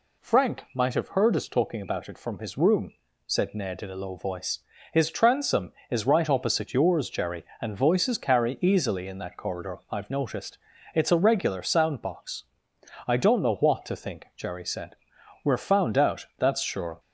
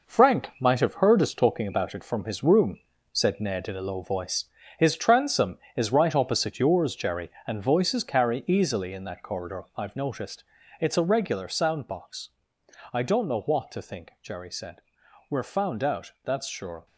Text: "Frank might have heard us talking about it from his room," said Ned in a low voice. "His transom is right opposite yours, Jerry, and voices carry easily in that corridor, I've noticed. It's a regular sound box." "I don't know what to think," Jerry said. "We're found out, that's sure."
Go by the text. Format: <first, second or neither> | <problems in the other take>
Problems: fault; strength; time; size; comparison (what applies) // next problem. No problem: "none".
first | gets quieter; strong; throughout; 7 dB